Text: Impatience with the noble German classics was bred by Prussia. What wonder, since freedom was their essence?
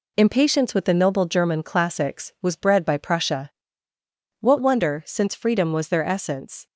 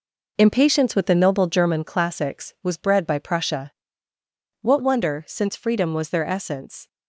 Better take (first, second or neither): first